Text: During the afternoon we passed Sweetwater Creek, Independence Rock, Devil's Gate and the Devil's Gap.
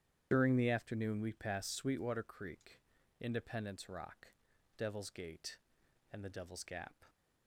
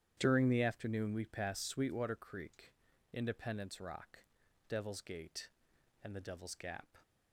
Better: second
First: loses the start of "During"; at 0.3 s; 65 ms // starts louder than the rest; strong; until 1.3 s; 10 dB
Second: starts louder than the rest; strong; until 1.1 s; 10 dB

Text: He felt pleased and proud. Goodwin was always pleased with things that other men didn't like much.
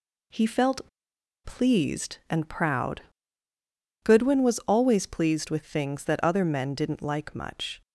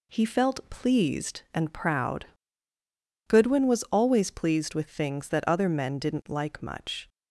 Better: second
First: pauses between "felt" and "pleased"; noticeable; at 0.8 s; 0.57 s long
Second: none

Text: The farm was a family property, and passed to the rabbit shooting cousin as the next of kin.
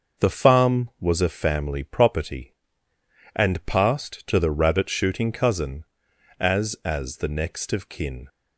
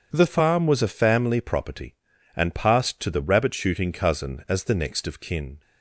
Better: second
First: starts louder than the rest; noticeable; until 1.3 s; 6 dB // says "as" twice; at 6.8 s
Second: starts louder than the rest; strong; until 1.1 s; 7 dB

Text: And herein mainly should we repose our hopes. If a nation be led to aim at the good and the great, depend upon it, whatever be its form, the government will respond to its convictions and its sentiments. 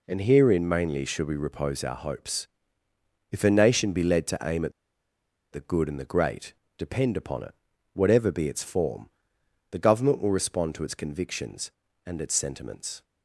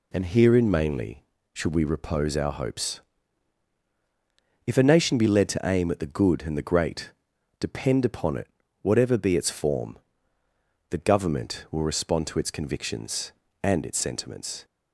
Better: second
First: pauses between "at" and "the"; noticeable; at 4.7 s; 0.81 s long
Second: none

